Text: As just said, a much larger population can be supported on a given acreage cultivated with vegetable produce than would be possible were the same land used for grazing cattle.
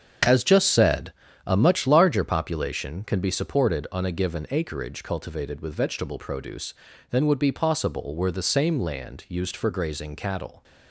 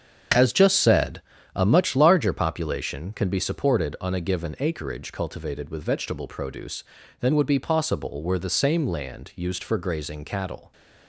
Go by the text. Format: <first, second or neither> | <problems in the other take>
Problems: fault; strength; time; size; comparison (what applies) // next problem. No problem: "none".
neither | starts louder than the rest; strong; the same in both